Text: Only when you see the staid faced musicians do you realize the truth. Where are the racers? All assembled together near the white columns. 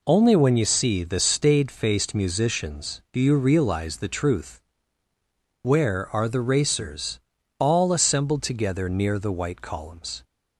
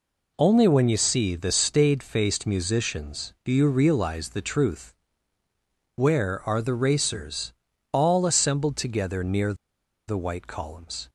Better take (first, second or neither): first